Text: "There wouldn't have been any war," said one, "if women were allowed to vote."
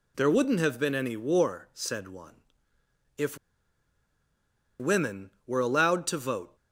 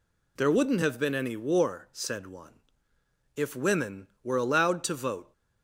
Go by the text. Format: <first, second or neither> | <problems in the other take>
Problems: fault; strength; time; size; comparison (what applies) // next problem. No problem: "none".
second | pauses between "if" and "women"; strong; at 3.3 s; 1.4 s long